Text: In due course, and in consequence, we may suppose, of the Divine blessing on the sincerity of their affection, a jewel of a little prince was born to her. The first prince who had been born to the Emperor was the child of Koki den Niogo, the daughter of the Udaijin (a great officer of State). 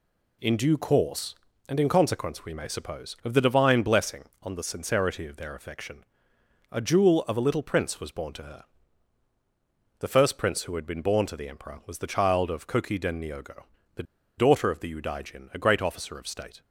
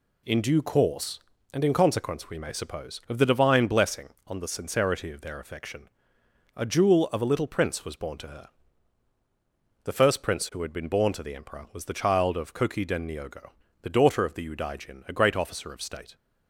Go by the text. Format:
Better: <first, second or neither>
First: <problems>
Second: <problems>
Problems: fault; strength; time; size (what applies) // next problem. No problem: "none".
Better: second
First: pauses between "the" and "daughter"; slight; at 14.0 s; 0.35 s long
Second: none